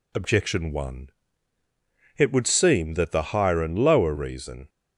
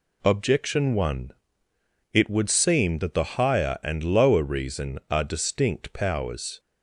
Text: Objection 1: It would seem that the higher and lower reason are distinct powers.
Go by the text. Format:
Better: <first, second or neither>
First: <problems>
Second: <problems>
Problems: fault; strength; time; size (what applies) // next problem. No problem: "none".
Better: second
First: stops before "are distinct powers"; at 4.6 s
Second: none